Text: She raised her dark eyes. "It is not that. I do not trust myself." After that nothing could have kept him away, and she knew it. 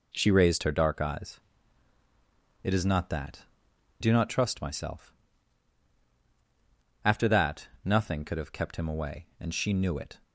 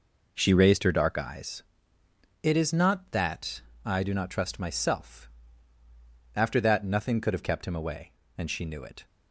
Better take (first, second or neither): second